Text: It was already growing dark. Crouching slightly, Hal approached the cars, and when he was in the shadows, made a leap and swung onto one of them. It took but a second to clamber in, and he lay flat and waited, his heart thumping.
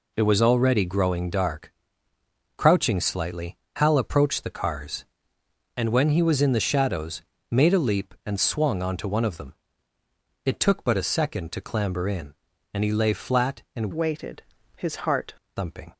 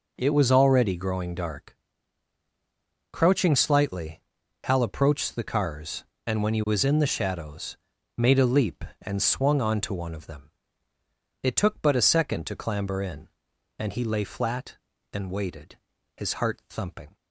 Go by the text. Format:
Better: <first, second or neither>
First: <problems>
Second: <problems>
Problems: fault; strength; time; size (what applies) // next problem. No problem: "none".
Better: second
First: changes voice from "waited" to "heart"; from 13.9 to 15.3 s; 1.4 s long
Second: none